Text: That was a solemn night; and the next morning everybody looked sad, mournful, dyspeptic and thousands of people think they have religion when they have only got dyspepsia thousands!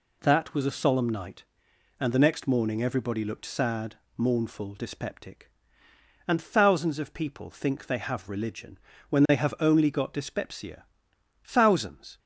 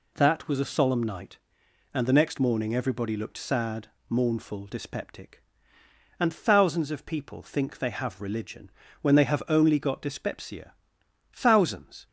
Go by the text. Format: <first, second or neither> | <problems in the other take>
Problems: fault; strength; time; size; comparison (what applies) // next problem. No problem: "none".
neither | pauses between "religion" and "when"; slight; the same in both // pauses between "dyspepsia" and "thousands"; noticeable; the same in both